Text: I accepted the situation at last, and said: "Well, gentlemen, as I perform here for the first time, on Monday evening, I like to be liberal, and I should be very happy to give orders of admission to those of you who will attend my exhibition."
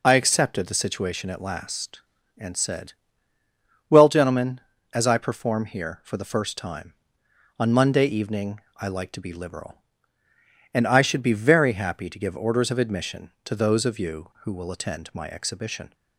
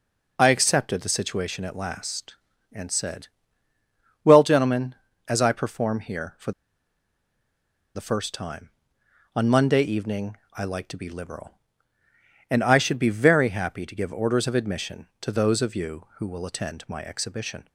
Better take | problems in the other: first | pauses between "for" and "the"; strong; at 6.5 s; 1.4 s long

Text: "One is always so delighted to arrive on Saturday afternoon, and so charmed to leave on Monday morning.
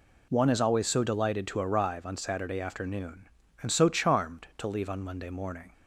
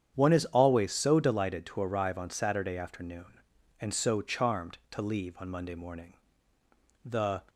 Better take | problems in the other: first | starts louder than the rest; strong; until 1.1 s; 8.5 dB // goes on to say "The"; slight; from 7.0 s on; 0.38 s long

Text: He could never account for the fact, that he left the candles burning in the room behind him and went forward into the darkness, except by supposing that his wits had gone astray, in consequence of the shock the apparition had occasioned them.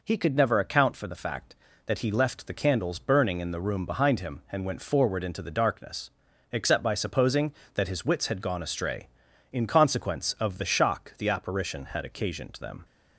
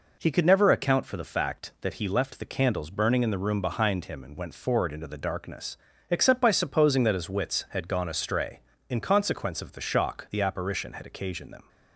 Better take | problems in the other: neither | none

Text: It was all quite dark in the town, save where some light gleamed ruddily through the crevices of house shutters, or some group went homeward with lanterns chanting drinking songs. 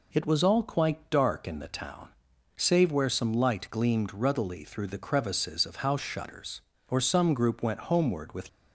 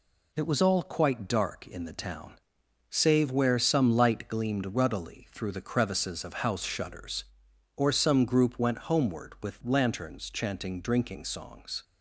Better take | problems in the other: second | stops before "lanterns chanting drinking songs"; at 8.4 s

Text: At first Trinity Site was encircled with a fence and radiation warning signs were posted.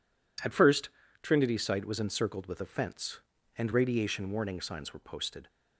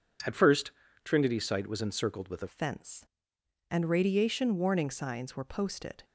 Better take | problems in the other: first | pauses between "first" and "Trinity"; slight; at 0.7 s; 0.32 s long; slight in the first // changes voice at "fence"; from 2.4 s on; 3.6 s long

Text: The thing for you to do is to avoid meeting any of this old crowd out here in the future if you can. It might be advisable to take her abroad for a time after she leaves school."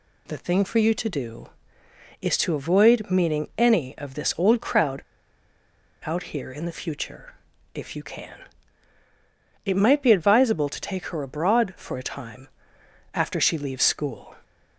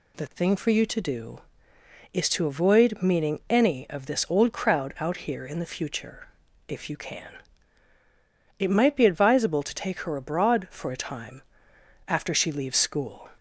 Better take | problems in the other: second | pauses between "crowd" and "out"; at 5.0 s; 1.0 s long // pauses between "future" and "if"; at 7.3 s; 0.42 s long; also in the second // pauses between "time" and "after"; noticeable; at 12.4 s; 0.66 s long; noticeable in the second

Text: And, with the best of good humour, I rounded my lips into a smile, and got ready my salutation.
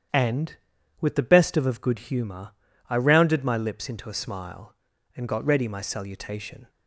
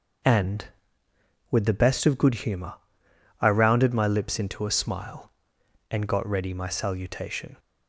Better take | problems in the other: second | starts louder than the rest; strong; until 1.5 s; 9 dB; also in the second // says "of" twice; at 1.6 s

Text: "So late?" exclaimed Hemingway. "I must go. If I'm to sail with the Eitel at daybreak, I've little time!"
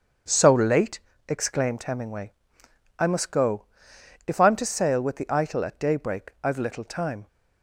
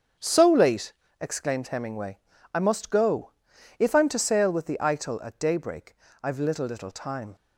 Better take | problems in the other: first | starts louder than the rest; until 1.4 s; 7 dB; strong in the first // says "little" twice; at 6.6 s

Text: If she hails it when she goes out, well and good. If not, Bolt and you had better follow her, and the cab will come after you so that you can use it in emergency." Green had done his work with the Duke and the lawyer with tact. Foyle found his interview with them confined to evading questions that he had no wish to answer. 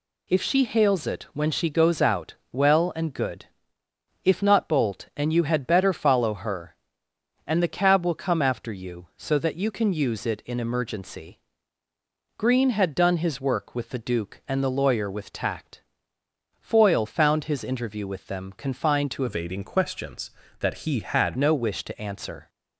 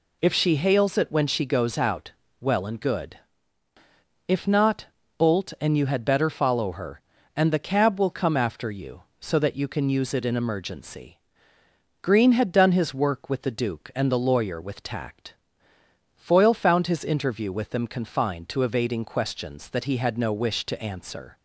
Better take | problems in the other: second | changes voice from "evading" to "had"; from 19.2 to 21.3 s; 2.1 s long

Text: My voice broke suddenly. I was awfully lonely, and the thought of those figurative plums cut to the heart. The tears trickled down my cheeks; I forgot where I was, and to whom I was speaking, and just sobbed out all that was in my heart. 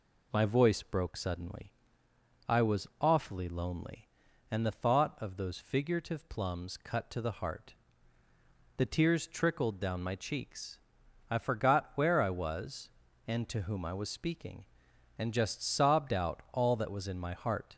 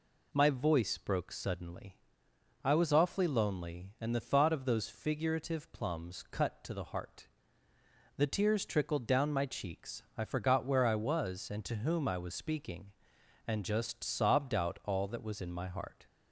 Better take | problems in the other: neither | none

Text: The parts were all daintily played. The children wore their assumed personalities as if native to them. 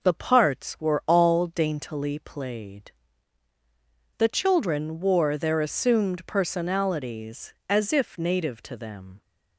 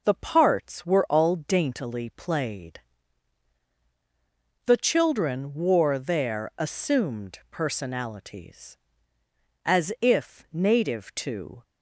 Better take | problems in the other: first | stops before "them"; at 11.6 s

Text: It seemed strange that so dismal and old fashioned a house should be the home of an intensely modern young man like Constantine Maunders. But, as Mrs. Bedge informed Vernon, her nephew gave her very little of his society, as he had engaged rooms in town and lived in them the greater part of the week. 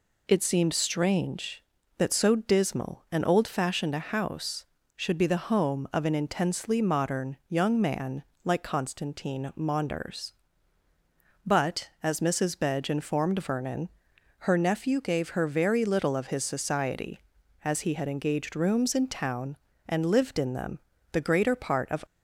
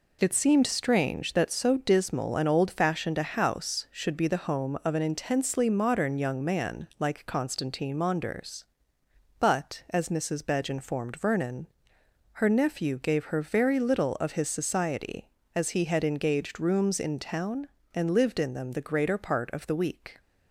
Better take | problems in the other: second | pauses between "man" and "like"; slight; at 8.2 s; 0.22 s long // pauses between "them" and "the"; slight; at 20.7 s; 0.32 s long // stops before "the week"; at 22.0 s

